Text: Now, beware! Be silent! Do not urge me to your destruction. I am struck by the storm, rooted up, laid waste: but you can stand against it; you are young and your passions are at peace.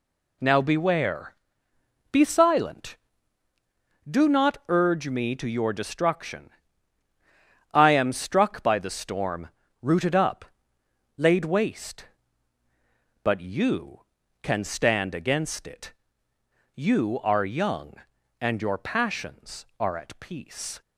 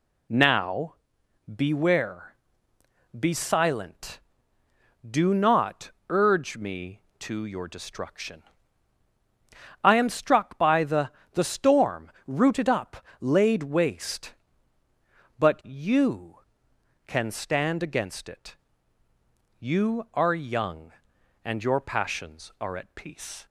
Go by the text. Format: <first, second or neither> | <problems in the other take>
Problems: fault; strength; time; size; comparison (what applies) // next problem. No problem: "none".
first | pauses between "not" and "urge"; slight; at 5.9 s; 0.16 s long // says "the" twice; at 11.3 s